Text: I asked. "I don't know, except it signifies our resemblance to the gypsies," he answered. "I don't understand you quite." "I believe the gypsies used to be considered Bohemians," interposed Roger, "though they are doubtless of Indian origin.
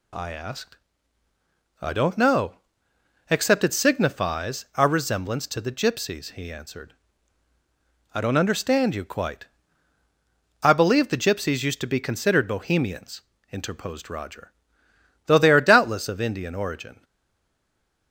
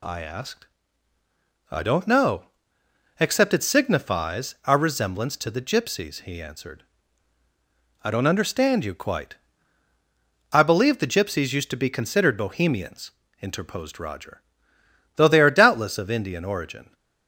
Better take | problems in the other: second | stays silent after the last word; from 17.0 s on; 1.1 s long

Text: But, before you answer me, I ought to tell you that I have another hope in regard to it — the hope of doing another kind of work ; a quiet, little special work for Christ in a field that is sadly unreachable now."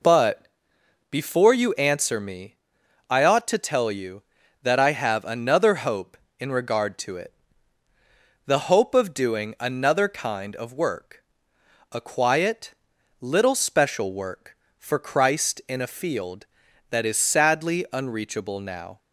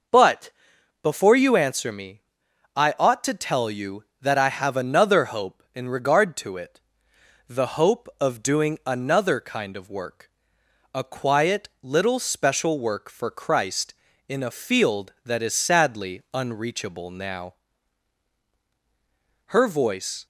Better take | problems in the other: first | goes on to say "Her voice"; noticeable; from 19.4 s on; 0.78 s long

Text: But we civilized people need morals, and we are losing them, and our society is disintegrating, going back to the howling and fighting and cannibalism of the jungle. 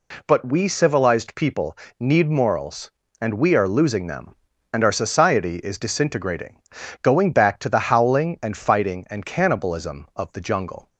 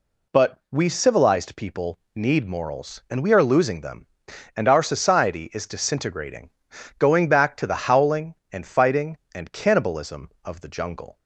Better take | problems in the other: neither | pauses between "people" and "need"; slight; the same in both

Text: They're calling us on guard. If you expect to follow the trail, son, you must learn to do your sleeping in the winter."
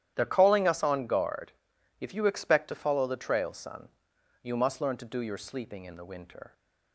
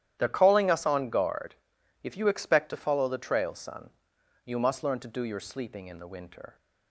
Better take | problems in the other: neither | starts louder than the rest; strong; the same in both

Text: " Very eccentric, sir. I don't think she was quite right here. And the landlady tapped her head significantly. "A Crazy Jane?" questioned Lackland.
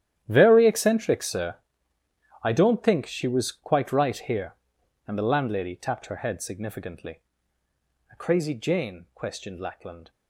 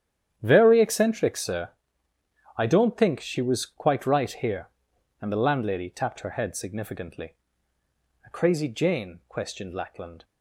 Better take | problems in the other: second | gets quieter; strong; throughout; 13.5 dB // starts louder than the rest; strong; until 1.1 s; 11 dB; strong in the second

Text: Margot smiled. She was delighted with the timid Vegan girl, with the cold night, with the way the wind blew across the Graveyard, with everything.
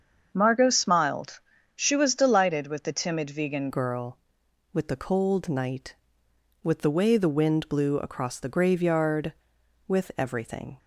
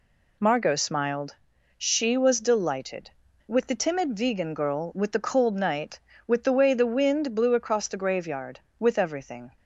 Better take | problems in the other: second | starts louder than the rest; until 1.3 s; 7 dB // changes voice at "girl"; from 3.7 s on; 7.0 s long

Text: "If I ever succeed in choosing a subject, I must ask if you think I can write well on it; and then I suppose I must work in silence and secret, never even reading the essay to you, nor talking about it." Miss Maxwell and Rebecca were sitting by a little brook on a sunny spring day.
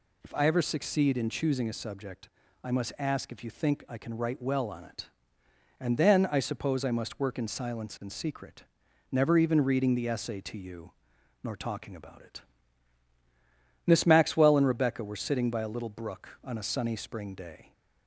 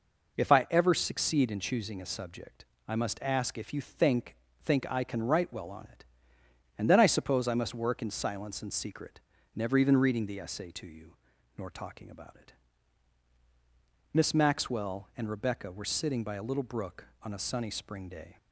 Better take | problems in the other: first | says "think" twice; at 4.6 s

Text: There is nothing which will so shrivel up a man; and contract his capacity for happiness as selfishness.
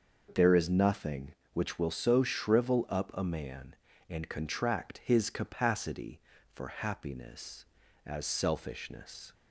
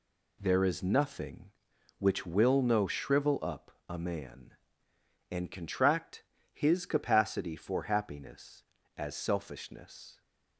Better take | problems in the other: first | says "no" for "so"; at 2.6 s // pauses between "up" and "a"; slight; at 3.7 s; 0.18 s long // pauses between "contract" and "his"; slight; at 6.2 s; 0.30 s long

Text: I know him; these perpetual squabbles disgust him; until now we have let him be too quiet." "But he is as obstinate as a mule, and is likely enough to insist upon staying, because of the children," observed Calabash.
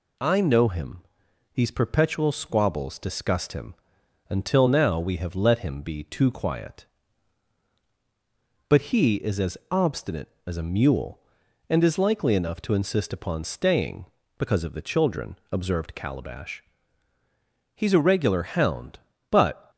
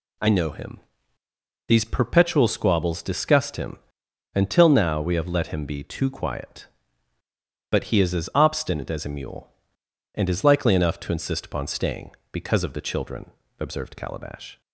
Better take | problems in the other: second | goes on to say "He's a regular hound but"; strong; from 17.7 s on; 1.9 s long

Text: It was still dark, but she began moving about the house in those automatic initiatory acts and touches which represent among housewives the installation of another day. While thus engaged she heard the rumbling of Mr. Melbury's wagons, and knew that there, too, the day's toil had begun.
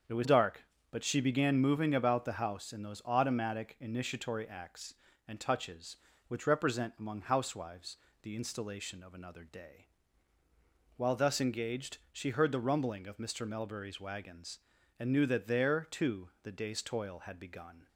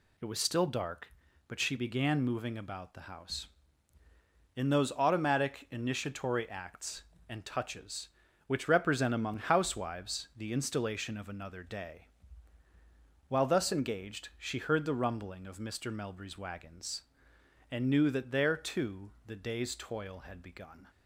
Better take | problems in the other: second | starts louder than the rest; until 1.3 s; 7 dB // skips "still"; at 0.2 s // pauses between "housewives" and "the"; slight; at 7.9 s; 0.24 s long

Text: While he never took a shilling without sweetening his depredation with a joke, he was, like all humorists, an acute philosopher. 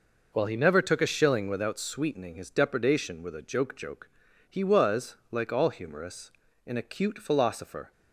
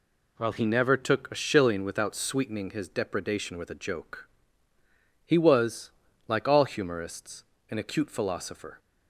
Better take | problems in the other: second | says "joke" twice; at 3.7 s

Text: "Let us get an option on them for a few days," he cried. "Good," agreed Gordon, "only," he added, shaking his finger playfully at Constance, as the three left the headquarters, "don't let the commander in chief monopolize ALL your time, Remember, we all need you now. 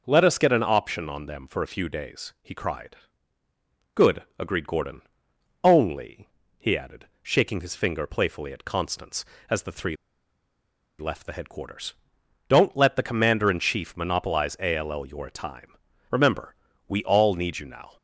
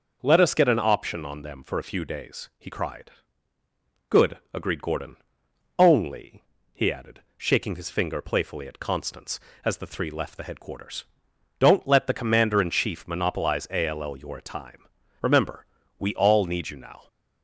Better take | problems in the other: second | starts louder than the rest; noticeable; until 1.0 s; 6 dB; noticeable in the second // pauses between "three" and "left"; at 9.9 s; 1.0 s long

